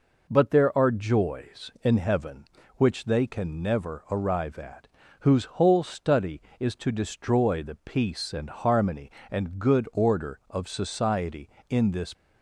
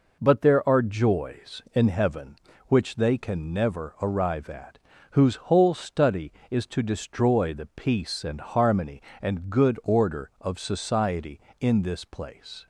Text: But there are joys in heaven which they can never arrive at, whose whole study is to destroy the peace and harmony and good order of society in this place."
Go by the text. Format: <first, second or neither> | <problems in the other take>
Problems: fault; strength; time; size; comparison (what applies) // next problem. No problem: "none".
second | stops before "place"; at 12.1 s